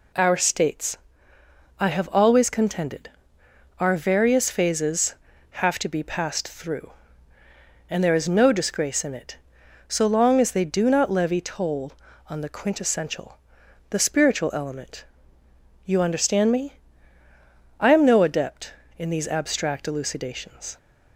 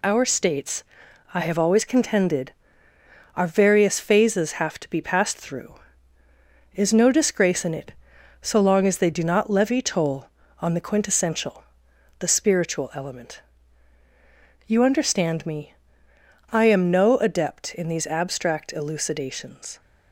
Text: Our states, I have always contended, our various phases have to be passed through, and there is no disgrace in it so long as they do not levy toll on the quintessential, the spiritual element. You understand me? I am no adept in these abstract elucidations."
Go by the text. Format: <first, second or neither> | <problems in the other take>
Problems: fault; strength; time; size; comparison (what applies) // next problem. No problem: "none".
first | skips "and there"; at 6.2 s